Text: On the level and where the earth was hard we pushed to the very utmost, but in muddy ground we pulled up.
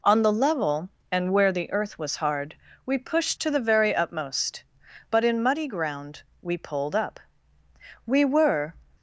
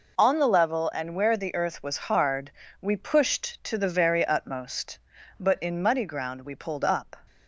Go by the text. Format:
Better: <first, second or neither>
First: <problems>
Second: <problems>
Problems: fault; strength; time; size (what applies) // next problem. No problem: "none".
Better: second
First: pauses between "hard" and "we"; slight; at 2.5 s; 0.32 s long // pauses between "ground" and "we"; slight; at 6.2 s; 0.18 s long // goes on to say "We were"; noticeable; from 8.0 s on; 0.68 s long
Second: pauses between "hard" and "we"; slight; at 2.5 s; 0.30 s long